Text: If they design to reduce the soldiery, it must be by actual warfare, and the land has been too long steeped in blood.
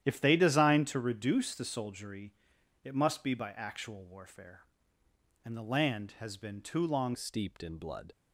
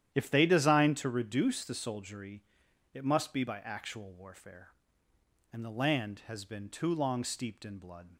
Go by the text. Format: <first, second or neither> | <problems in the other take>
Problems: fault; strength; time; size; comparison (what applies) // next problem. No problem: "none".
second | starts louder than the rest; strong; until 1.0 s; 10.5 dB; strong in the second // changes voice at "steeped"; from 7.1 s on; 1.0 s long